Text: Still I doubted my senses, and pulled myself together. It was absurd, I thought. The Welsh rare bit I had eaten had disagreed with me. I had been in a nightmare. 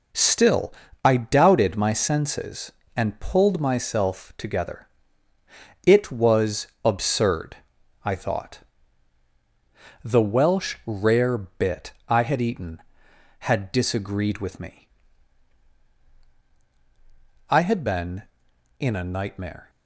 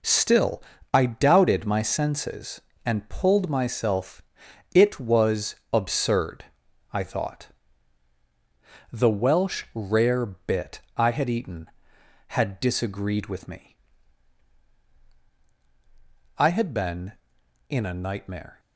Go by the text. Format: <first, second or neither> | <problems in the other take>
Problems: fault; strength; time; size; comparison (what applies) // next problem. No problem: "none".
first | pauses between "Still" and "I"; slight; at 0.6 s; 0.30 s long; slight in the first // skips "together"; at 4.4 s // pauses between "was" and "absurd"; slight; at 5.5 s; 0.16 s long; slight in the first // pauses between "bit" and "I"; slight; at 10.8 s; 0.16 s long; slight in the first